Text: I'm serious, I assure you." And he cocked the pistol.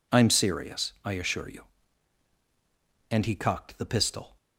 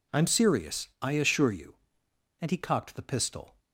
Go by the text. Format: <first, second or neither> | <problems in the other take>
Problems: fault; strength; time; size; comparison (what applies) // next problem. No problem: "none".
neither | none